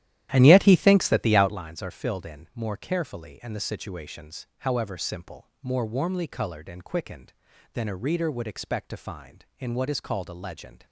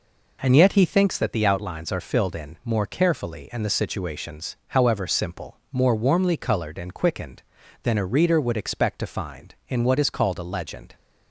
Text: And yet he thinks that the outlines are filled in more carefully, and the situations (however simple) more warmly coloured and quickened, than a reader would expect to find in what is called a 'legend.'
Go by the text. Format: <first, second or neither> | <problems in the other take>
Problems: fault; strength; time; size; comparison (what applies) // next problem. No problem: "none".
second | starts louder than the rest; strong; until 1.7 s; 12.5 dB